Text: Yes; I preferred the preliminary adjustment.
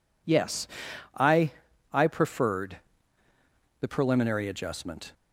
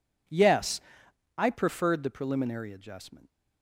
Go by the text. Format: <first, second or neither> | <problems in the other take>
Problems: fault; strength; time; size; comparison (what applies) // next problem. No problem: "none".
second | says "I" twice; at 1.9 s // pauses between "preferred" and "the"; at 2.7 s; 1.0 s long